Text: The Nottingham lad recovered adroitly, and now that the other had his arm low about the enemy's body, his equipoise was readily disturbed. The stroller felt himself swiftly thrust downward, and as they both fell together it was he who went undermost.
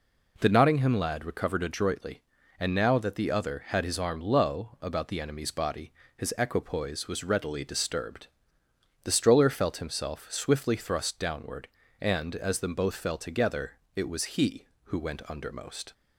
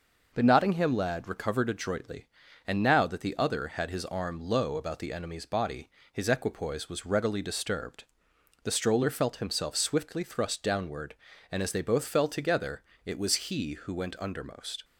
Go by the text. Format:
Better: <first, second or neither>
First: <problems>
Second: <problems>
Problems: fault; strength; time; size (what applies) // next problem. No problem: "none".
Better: second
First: says "them" for "they"; at 12.5 s // pauses between "together" and "it"; slight; at 13.7 s; 0.22 s long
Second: pauses between "together" and "it"; slight; at 12.8 s; 0.22 s long